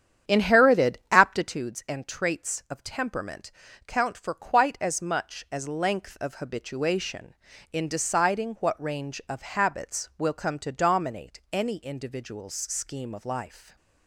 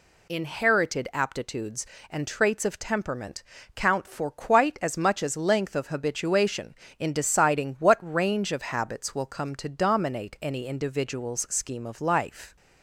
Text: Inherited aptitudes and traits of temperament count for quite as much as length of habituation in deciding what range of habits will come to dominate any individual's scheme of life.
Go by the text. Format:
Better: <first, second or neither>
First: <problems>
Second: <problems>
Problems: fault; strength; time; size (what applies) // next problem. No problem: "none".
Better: second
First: starts louder than the rest; strong; until 1.6 s; 9 dB // pauses between "temperament" and "count"; slight; at 3.5 s; 0.34 s long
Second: pauses between "temperament" and "count"; slight; at 3.4 s; 0.32 s long